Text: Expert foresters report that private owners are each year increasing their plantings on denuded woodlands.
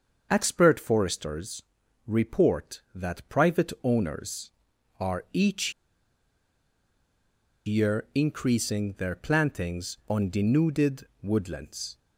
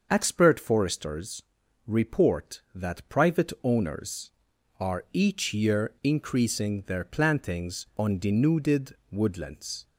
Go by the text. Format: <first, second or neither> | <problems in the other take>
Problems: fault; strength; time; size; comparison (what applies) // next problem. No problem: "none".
second | starts louder than the rest; until 1.3 s; 6.5 dB; also in the second // pauses between "foresters" and "report"; noticeable; at 1.6 s; 0.46 s long; noticeable in the second // pauses between "each" and "year"; strong; at 5.7 s; 1.9 s long // pauses between "denuded" and "woodlands"; slight; at 11.0 s; 0.16 s long; slight in the second